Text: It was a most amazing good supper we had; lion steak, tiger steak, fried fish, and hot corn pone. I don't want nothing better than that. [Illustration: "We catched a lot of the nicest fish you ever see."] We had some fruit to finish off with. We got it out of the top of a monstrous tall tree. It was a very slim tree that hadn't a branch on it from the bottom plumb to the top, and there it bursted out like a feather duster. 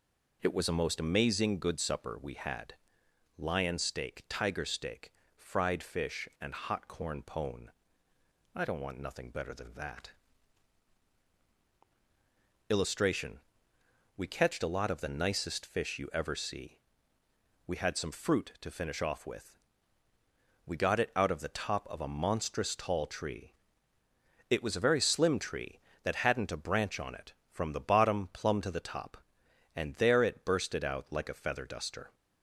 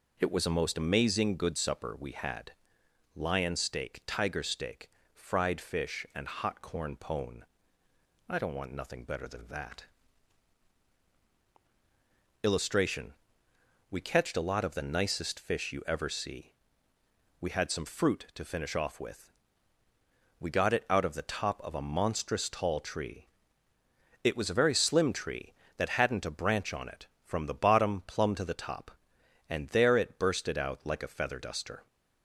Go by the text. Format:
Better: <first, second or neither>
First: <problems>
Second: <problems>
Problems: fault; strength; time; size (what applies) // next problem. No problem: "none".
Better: neither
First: none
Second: none